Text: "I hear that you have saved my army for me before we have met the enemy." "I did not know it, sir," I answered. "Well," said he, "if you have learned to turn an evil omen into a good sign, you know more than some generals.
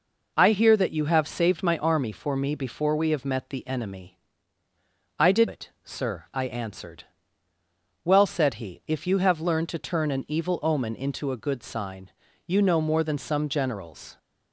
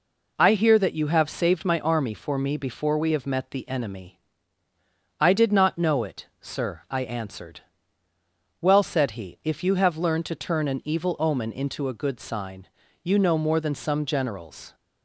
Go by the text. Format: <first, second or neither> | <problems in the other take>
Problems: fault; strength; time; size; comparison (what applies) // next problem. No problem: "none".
second | skips "not know"; at 5.4 s